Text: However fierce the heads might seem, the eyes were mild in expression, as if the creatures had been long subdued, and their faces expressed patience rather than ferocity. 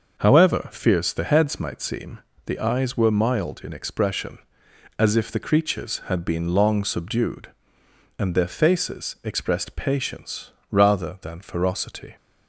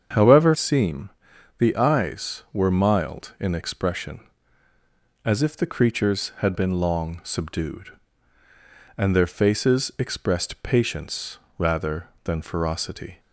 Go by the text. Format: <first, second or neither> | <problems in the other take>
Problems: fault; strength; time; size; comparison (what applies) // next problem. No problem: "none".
first | starts louder than the rest; strong; until 1.6 s; 7 dB; noticeable in the first // skips "fierce the heads might"; at 0.5 s // pauses between "patience" and "rather"; slight; at 11.3 s; 0.22 s long; slight in the first